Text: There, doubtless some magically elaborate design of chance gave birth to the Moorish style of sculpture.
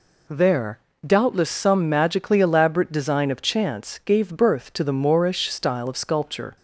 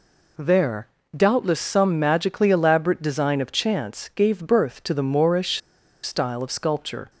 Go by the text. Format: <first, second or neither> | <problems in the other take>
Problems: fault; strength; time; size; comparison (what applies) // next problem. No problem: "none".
first | pauses between "Moorish" and "style"; at 5.6 s; 0.45 s long